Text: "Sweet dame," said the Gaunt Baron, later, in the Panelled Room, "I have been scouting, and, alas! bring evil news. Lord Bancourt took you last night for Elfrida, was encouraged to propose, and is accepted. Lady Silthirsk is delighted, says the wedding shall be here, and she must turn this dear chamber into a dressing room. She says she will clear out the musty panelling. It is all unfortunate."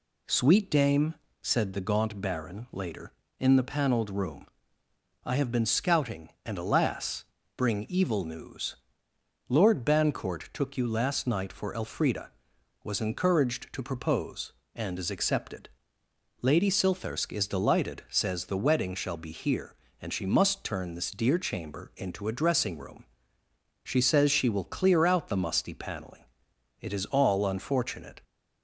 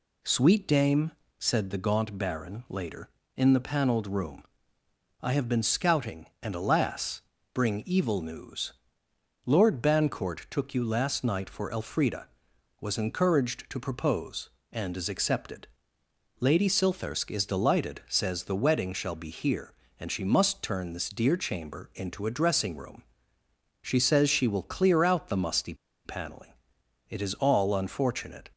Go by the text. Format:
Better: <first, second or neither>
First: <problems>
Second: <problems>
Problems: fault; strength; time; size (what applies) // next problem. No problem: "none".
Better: first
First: none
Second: pauses between "musty" and "panelling"; slight; at 25.7 s; 0.30 s long